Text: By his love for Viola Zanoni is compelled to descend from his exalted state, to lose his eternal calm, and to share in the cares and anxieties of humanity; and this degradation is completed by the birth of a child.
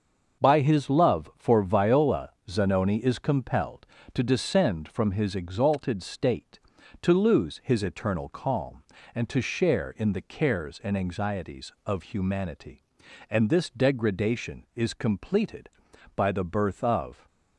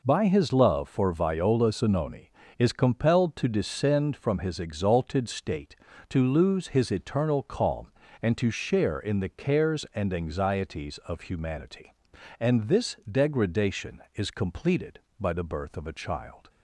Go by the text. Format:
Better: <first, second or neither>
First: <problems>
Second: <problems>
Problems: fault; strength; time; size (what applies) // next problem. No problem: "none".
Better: second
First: starts louder than the rest; until 1.4 s; 6.5 dB // pauses between "Viola" and "Zanoni"; slight; at 2.3 s; 0.16 s long // stops before "a child"; at 17.2 s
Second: none